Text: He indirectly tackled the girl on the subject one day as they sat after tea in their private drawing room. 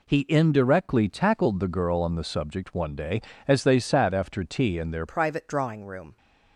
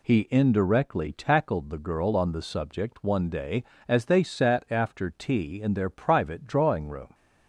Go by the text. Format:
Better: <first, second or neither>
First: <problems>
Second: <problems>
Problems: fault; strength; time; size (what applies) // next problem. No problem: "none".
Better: second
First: changes voice at "private"; from 5.0 s on; 1.1 s long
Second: none